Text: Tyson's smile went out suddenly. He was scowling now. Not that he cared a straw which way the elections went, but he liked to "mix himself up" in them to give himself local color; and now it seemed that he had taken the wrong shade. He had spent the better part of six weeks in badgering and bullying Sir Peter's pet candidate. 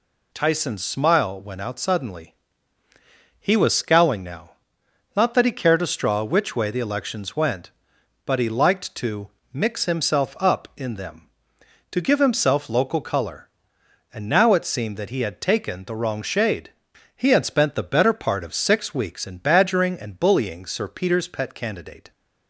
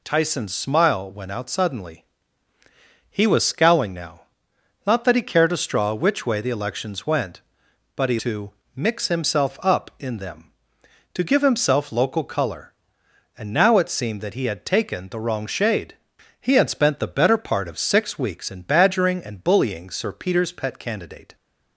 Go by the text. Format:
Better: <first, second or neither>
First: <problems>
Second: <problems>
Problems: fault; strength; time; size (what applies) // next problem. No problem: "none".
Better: first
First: pauses between "to" and "mix"; slight; at 9.2 s; 0.24 s long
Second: skips "liked"; at 8.1 s // pauses between "to" and "mix"; slight; at 8.5 s; 0.24 s long